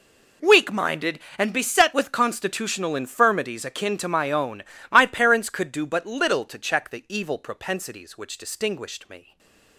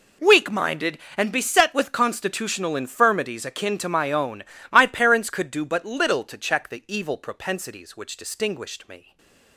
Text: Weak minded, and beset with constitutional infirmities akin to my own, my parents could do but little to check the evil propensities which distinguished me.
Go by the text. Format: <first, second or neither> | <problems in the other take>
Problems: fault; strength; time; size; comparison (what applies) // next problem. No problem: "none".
neither | stays silent after the last word; slight; the same in both